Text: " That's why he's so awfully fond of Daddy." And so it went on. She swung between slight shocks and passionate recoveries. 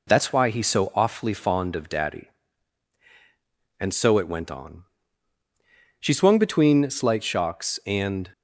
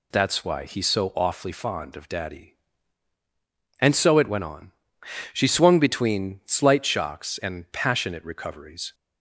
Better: second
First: stops before "passionate recoveries"; at 8.3 s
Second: none

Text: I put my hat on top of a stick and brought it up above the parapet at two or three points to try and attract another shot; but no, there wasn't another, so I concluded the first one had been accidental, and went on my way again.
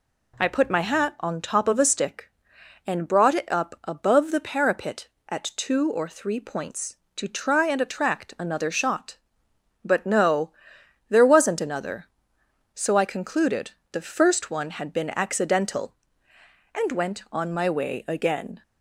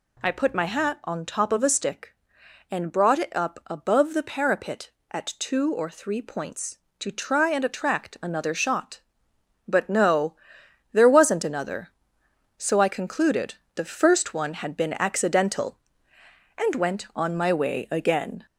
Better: first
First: pauses between "concluded" and "the"; slight; at 13.7 s; 0.20 s long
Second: gets louder; slight; throughout; 3.5 dB // pauses between "concluded" and "the"; slight; at 13.5 s; 0.20 s long

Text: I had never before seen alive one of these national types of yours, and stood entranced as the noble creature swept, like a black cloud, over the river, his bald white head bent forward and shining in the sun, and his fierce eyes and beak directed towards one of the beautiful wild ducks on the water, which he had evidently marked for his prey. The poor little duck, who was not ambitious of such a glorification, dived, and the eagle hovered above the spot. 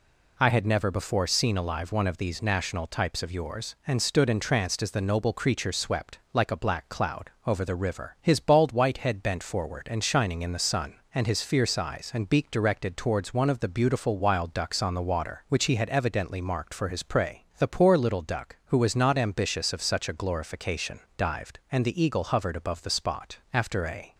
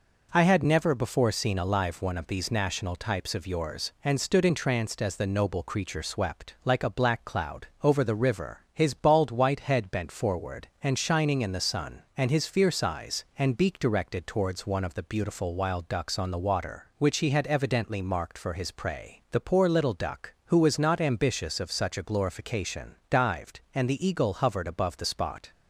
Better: second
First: goes on to say "After a"; noticeable; from 23.5 s on; 0.62 s long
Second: none

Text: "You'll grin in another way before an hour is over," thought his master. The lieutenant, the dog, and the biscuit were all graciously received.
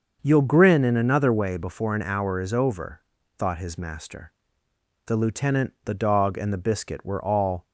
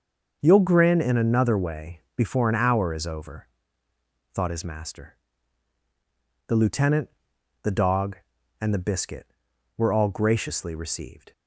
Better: second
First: starts louder than the rest; until 1.2 s; 6.5 dB // stops before "graciously received"; at 7.6 s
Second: starts louder than the rest; until 1.4 s; 6.5 dB

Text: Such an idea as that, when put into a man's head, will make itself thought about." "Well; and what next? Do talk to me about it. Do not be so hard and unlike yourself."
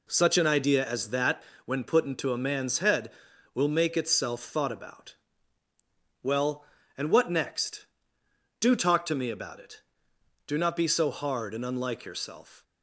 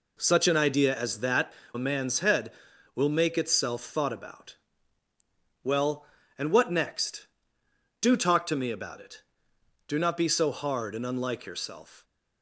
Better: first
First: none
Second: skips "when put into"; at 1.6 s

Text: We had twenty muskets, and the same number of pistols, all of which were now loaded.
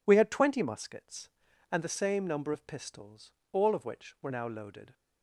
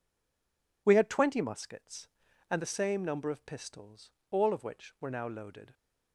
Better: first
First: none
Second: stays silent before the first word; slight; until 0.8 s; 0.8 s long

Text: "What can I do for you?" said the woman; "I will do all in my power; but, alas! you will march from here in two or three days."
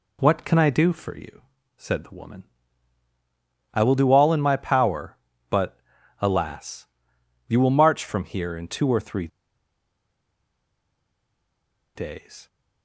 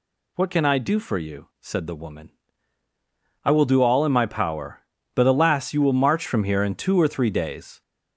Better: second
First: pauses between "three" and "days"; strong; at 9.2 s; 2.6 s long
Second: none

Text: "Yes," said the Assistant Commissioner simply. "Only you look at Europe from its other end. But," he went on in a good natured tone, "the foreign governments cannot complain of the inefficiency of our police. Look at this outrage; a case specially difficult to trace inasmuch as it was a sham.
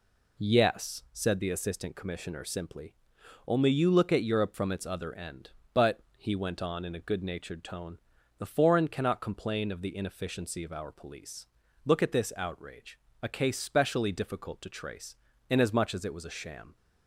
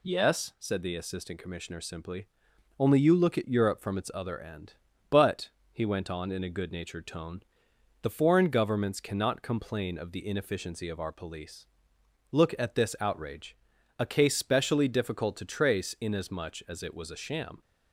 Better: second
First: skips "governments"; at 8.8 s // pauses between "trace" and "inasmuch"; slight; at 15.1 s; 0.34 s long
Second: none

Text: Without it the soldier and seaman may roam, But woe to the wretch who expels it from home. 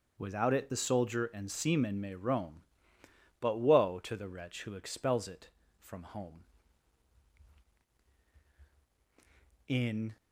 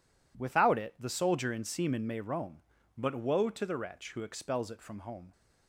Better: second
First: starts louder than the rest; until 1.1 s; 6.5 dB // goes on to say "In"; slight; from 9.6 s on; 0.48 s long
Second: none

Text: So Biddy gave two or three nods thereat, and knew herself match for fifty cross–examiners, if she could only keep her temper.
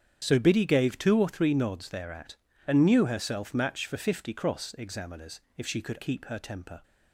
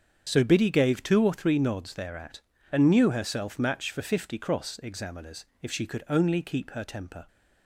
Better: second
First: starts louder than the rest; strong; until 1.2 s; 8.5 dB // skips "only"; at 5.9 s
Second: starts louder than the rest; strong; until 1.2 s; 7.5 dB

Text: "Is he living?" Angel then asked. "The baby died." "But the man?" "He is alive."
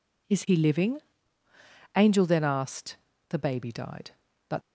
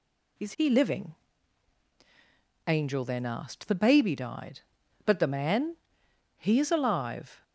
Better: second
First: stops before "the man He is alive"; at 4.6 s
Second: none

